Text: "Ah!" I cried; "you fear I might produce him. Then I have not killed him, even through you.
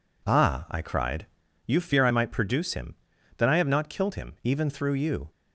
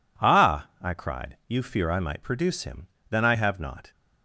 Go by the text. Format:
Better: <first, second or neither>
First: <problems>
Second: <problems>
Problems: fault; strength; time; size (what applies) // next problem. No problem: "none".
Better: first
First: none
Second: stops before "killed him even through you"; at 3.9 s